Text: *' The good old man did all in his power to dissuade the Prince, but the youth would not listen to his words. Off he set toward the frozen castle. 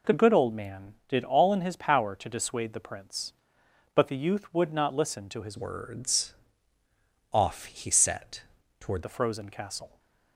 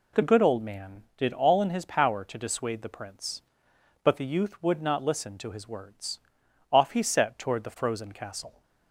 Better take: second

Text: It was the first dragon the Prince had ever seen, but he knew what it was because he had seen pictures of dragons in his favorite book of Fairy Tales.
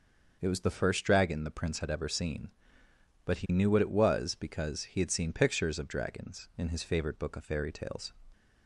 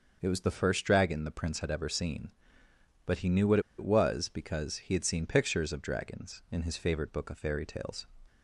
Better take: first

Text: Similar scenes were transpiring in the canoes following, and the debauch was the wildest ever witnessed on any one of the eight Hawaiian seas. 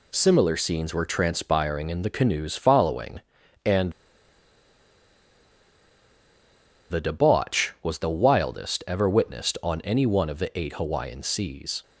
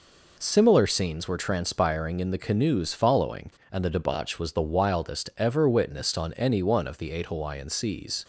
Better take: second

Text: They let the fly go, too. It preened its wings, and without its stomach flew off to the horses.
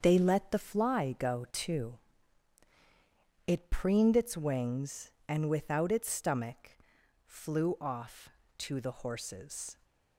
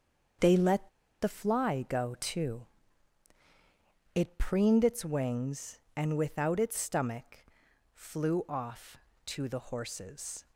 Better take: first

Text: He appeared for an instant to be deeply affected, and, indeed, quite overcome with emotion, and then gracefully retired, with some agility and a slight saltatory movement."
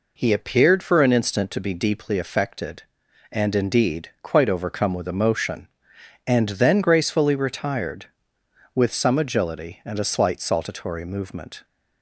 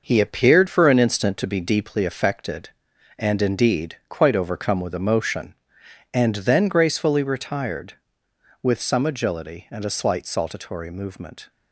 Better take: first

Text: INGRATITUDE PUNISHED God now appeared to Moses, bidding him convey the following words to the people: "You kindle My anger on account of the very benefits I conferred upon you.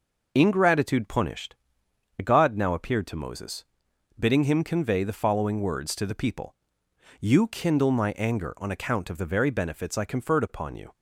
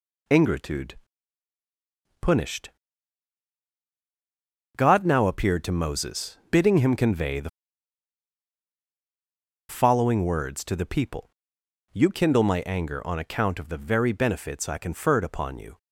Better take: first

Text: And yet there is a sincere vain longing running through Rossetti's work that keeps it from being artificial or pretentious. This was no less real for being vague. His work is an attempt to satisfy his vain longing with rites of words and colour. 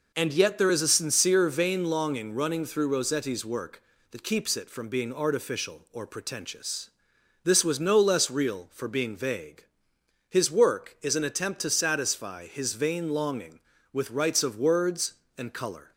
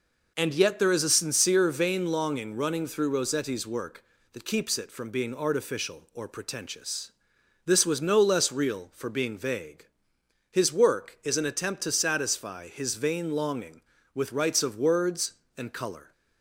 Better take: neither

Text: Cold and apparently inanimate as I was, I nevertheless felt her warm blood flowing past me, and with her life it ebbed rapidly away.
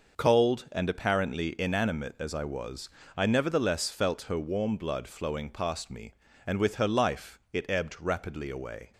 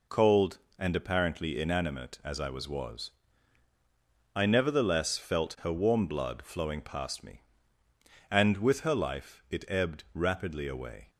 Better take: first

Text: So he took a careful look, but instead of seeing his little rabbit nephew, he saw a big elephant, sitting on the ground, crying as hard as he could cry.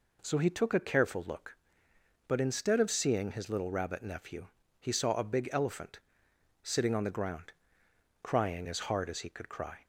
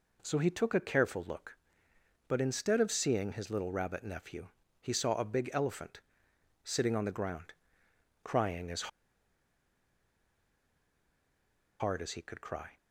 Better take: first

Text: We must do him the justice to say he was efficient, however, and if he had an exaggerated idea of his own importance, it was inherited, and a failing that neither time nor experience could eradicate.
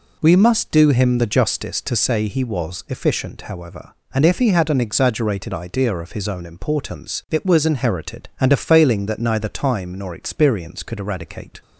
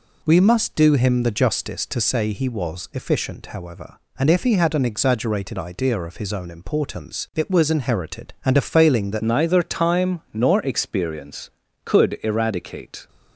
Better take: first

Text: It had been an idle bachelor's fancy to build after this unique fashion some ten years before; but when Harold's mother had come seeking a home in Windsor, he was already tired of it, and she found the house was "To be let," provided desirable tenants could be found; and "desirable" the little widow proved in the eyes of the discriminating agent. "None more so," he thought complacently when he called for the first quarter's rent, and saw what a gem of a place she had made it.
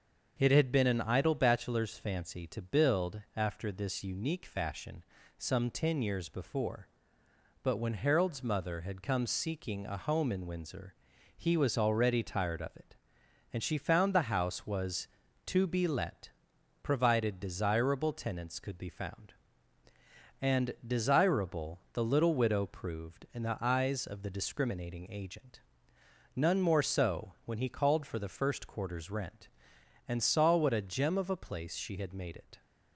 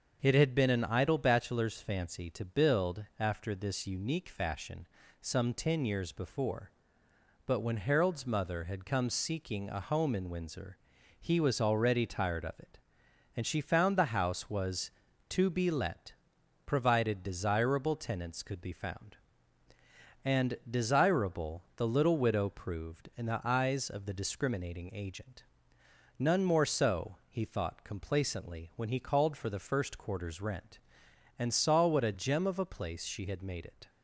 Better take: second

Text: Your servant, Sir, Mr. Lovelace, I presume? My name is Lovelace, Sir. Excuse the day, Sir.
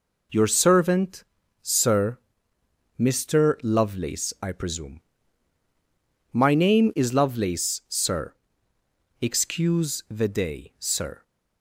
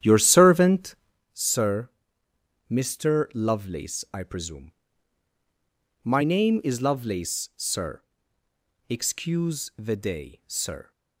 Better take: first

